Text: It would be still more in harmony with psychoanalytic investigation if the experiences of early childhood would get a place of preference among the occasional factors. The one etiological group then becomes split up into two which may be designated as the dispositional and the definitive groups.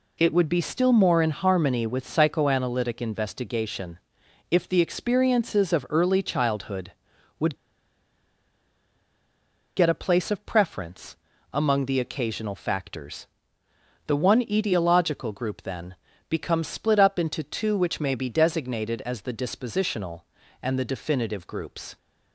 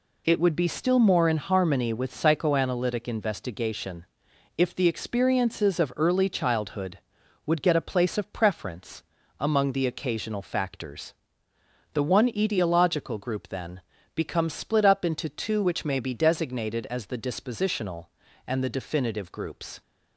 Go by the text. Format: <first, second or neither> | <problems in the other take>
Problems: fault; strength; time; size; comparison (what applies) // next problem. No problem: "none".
second | pauses between "investigation" and "if"; noticeable; at 3.9 s; 0.52 s long; noticeable in the second // pauses between "would" and "get"; strong; at 7.5 s; 2.2 s long // pauses between "preference" and "among"; slight; at 11.1 s; 0.36 s long; slight in the second // pauses between "then" and "becomes"; slight; at 15.9 s; 0.34 s long; slight in the second